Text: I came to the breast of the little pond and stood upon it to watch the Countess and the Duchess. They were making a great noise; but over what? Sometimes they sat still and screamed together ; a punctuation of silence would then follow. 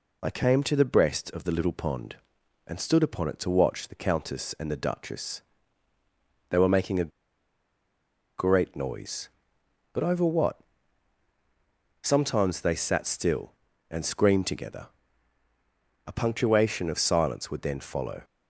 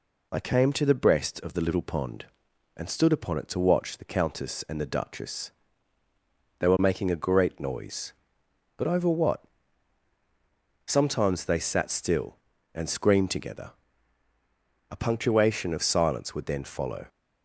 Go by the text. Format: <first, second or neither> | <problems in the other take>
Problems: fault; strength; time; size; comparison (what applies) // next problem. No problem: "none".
second | pauses between "a" and "great"; strong; at 7.1 s; 1.3 s long